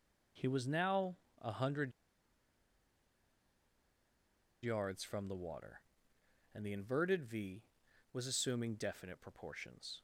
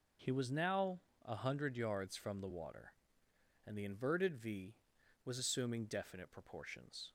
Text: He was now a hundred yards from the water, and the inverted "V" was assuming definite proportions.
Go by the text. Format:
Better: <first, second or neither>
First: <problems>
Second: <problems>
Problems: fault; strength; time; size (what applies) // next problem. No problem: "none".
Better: second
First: pauses between "now" and "a"; slight; at 1.1 s; 0.24 s long // pauses between "hundred" and "yards"; strong; at 1.9 s; 2.7 s long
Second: pauses between "now" and "a"; slight; at 1.0 s; 0.24 s long